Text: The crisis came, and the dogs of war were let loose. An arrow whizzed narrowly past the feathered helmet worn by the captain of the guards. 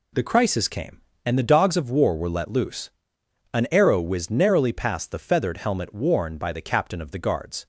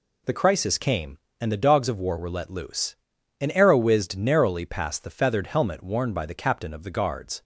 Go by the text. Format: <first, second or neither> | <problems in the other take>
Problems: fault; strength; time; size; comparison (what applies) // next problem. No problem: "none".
neither | none